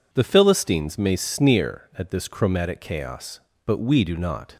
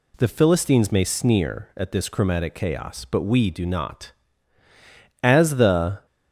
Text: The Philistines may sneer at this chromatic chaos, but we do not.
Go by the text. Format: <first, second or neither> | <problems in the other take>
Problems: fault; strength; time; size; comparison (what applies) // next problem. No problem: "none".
first | goes on to say "As the"; noticeable; from 5.2 s on; 0.84 s long